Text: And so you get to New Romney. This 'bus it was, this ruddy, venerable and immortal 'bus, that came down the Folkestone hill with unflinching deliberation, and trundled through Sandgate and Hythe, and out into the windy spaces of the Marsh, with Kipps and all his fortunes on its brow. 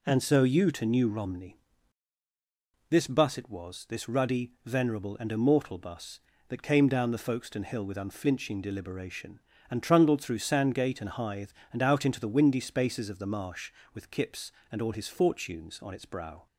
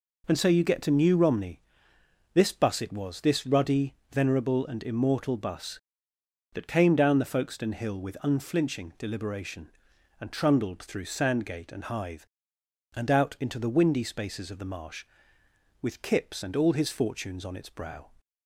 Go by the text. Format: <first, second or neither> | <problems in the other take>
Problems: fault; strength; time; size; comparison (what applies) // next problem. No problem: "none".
second | skips "get"; at 0.7 s